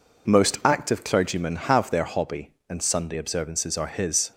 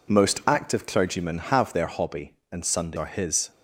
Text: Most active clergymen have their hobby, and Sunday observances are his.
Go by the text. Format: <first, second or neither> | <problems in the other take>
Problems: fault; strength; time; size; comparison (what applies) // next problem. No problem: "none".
first | skips "observances"; at 2.9 s